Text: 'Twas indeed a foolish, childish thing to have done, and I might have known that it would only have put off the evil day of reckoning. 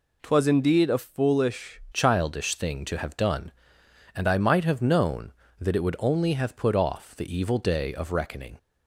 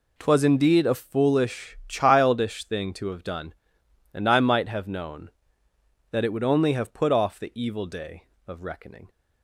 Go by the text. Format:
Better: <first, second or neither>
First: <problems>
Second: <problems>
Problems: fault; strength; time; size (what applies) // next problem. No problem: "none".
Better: second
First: changes voice at "childish"; from 1.9 s on; 6.6 s long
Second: none